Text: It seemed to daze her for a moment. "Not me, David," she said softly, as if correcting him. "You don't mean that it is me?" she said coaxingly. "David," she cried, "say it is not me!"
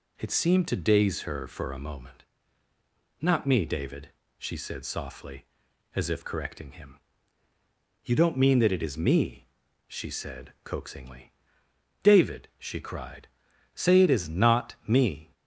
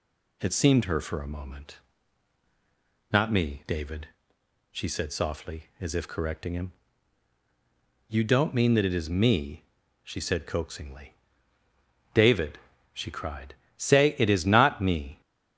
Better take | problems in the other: first | skips "to daze"; at 0.8 s

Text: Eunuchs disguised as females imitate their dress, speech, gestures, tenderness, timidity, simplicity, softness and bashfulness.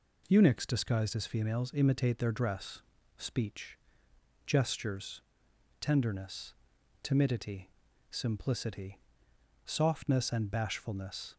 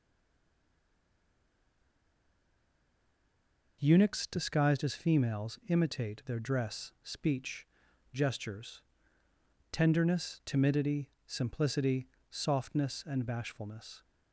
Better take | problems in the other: first | stays silent before the first word; strong; until 3.8 s; 3.8 s long

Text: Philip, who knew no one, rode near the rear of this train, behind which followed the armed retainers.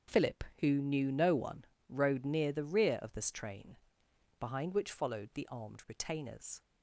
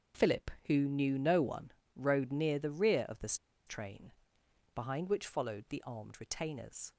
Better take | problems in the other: first | starts louder than the rest; strong; until 1.3 s; 7.5 dB; strong in the first // pauses between "this" and "train"; slight; at 3.3 s; 0.31 s long

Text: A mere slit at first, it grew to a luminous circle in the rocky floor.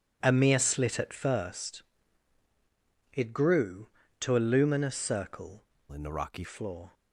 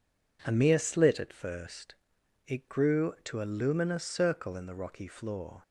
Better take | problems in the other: second | changes voice from "in" to "rocky"; from 5.9 to 6.4 s; 0.5 s long

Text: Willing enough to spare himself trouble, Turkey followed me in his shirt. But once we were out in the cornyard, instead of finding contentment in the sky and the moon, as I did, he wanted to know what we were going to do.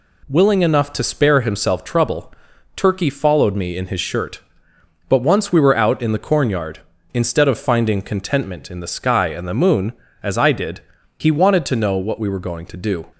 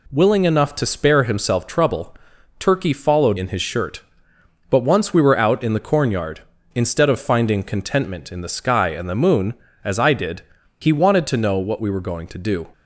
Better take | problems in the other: first | skips "me"; at 3.3 s

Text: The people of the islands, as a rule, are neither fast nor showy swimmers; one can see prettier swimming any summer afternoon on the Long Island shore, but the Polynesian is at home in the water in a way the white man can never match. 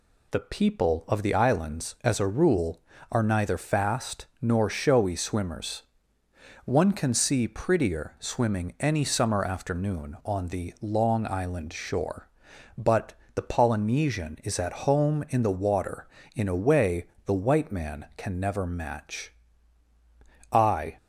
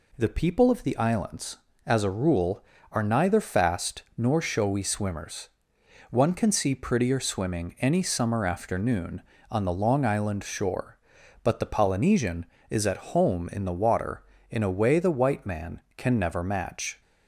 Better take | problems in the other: second | pauses between "but" and "the"; slight; at 13.1 s; 0.22 s long // pauses between "way" and "the"; slight; at 17.0 s; 0.22 s long // goes on to say "I"; slight; from 20.5 s on; 0.46 s long

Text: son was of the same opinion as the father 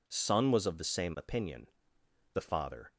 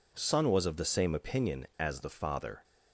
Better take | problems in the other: second | skips "as"; at 1.9 s

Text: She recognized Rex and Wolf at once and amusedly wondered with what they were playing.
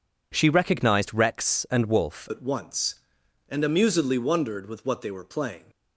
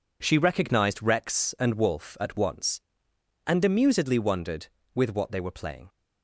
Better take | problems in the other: second | changes voice at "at"; from 2.2 s on; 3.4 s long

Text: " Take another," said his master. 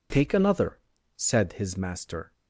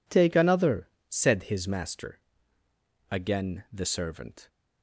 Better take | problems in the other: first | goes on to say "Again the servant"; from 3.1 s on; 1.3 s long

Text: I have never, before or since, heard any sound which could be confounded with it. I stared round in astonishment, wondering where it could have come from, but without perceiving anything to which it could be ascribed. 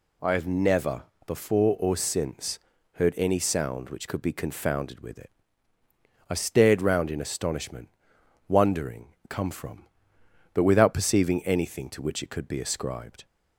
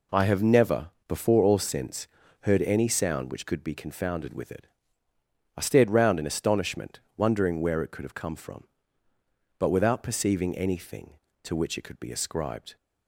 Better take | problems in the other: second | skips "where it could have"; at 9.2 s

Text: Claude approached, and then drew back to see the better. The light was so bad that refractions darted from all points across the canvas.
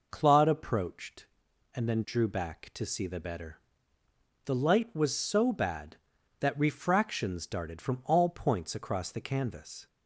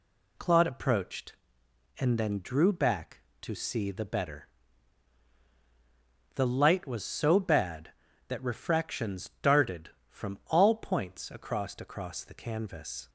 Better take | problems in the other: first | says "across" twice; at 11.7 s

